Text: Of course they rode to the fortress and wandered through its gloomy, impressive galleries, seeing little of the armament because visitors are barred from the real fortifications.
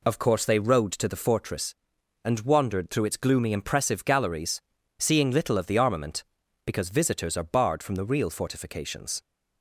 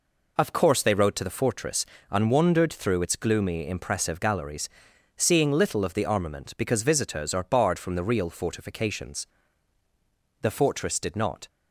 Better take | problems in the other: first | goes on to say "The fortress did not"; noticeable; from 10.3 s on; 1.0 s long

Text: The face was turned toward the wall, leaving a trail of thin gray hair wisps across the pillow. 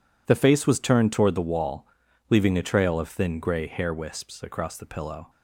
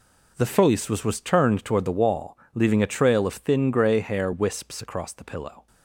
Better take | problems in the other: first | says "was" twice; at 1.0 s

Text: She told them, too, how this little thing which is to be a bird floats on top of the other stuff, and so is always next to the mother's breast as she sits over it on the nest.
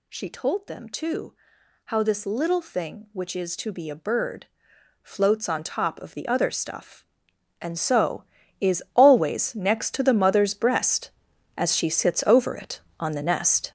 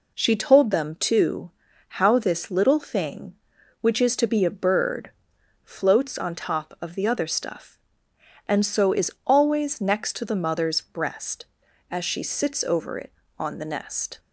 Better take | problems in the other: second | gets louder; strong; throughout; 9.5 dB // pauses between "bird" and "floats"; noticeable; at 4.4 s; 0.56 s long; noticeable in the second

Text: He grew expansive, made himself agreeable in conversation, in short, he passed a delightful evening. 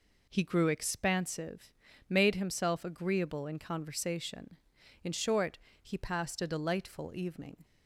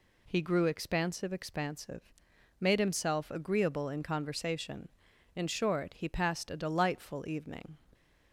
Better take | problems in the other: first | says "expansive" twice; at 1.3 s

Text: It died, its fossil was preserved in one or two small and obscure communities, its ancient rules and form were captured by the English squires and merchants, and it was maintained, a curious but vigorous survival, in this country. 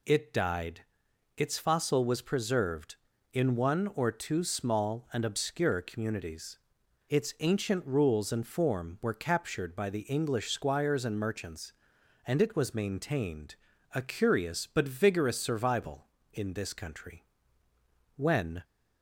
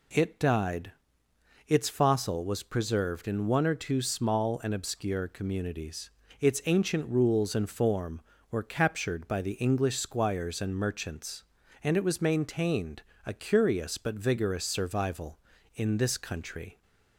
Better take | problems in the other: second | goes on to say "When"; slight; from 18.1 s on; 0.46 s long

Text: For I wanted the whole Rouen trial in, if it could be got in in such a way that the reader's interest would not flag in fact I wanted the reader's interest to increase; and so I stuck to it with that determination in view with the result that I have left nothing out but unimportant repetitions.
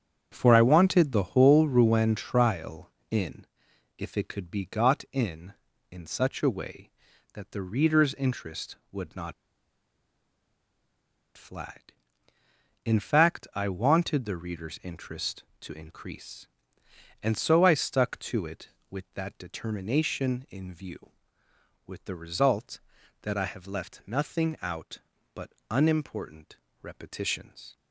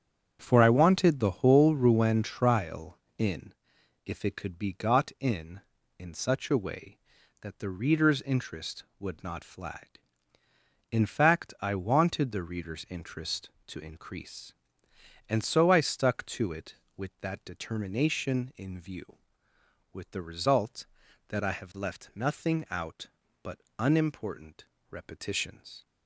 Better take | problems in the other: second | starts louder than the rest; strong; until 1.3 s; 8 dB; strong in the second // pauses between "not" and "flag"; strong; at 9.3 s; 2.0 s long // pauses between "but" and "unimportant"; slight; at 25.5 s; 0.18 s long; slight in the second // pauses between "unimportant" and "repetitions"; slight; at 26.5 s; 0.26 s long; slight in the second

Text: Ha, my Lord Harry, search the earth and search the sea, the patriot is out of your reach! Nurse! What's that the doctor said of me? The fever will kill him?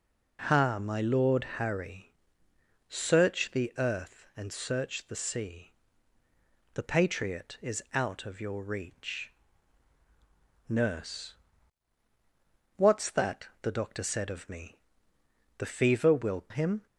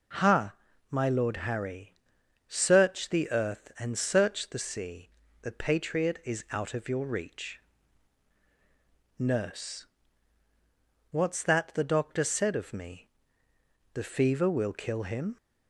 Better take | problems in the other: second | pauses between "that" and "the"; slight; at 13.4 s; 0.16 s long // skips "kill"; at 16.4 s

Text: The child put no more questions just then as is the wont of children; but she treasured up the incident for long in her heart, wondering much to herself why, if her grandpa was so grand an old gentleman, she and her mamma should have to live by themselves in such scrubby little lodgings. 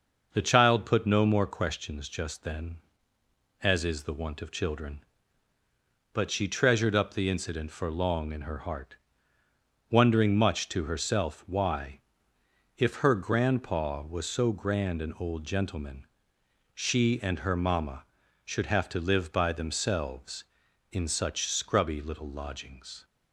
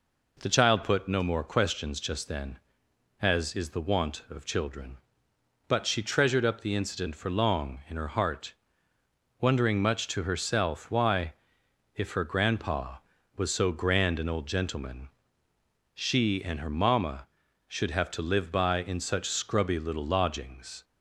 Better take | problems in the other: first | skips "themselves"; at 18.8 s

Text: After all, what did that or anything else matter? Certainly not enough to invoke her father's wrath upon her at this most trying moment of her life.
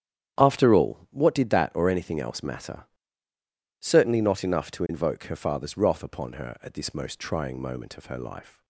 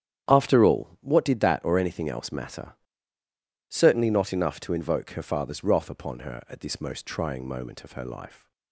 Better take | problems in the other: neither | starts louder than the rest; strong; the same in both

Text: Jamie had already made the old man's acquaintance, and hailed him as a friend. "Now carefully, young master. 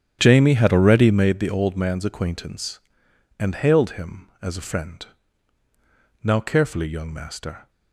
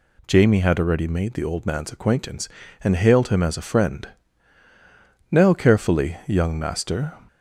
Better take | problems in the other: second | starts louder than the rest; strong; until 1.3 s; 9.5 dB

